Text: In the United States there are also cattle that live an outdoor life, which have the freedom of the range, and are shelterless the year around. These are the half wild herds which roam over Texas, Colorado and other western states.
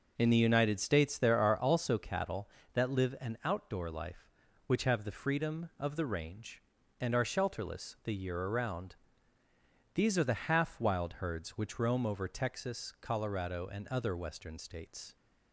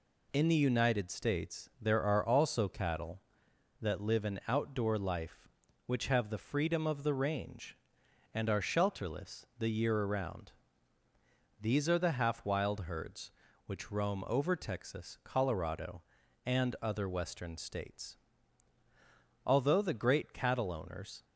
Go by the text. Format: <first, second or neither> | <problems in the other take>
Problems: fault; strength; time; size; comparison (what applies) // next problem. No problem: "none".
first | goes on to say "Although the great cattle owners"; strong; from 19.4 s on; 1.8 s long